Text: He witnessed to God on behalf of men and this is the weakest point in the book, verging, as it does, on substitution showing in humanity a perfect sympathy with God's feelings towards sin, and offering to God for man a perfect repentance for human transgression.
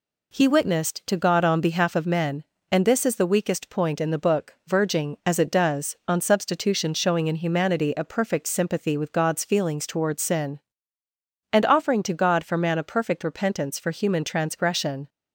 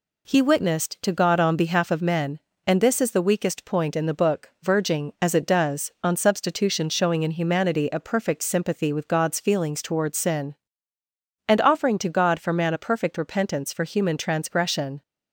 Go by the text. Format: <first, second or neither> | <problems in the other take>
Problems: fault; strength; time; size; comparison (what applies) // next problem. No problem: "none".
neither | none